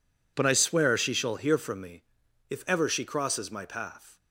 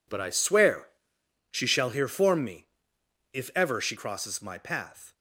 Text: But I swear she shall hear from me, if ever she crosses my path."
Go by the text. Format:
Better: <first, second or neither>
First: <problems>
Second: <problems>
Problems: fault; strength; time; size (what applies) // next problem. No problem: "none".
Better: first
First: none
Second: pauses between "swear" and "she"; noticeable; at 0.8 s; 0.64 s long // says "form" for "from"; at 2.0 s